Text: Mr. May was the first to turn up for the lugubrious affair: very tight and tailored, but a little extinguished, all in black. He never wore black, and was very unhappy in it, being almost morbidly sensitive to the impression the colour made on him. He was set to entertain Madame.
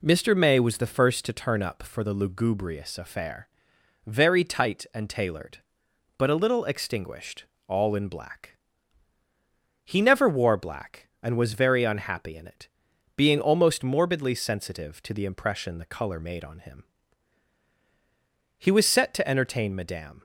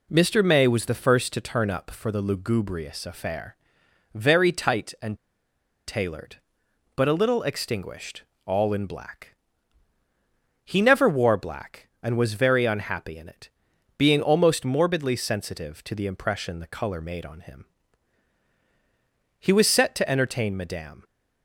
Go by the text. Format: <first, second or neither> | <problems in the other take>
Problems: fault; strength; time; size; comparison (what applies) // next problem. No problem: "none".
first | pauses between "and" and "tailored"; noticeable; at 5.1 s; 0.71 s long